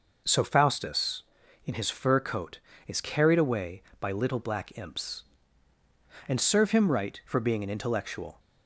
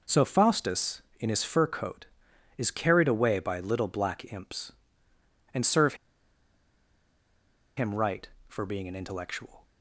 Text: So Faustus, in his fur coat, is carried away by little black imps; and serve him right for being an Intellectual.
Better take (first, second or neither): first